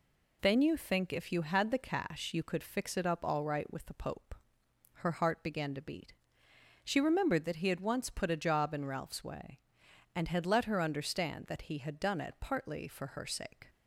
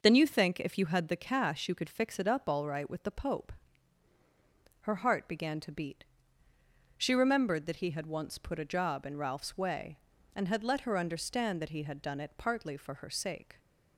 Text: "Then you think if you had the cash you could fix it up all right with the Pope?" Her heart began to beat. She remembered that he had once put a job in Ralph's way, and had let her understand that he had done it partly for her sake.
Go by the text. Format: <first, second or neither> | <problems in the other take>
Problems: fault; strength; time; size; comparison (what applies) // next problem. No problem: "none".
neither | none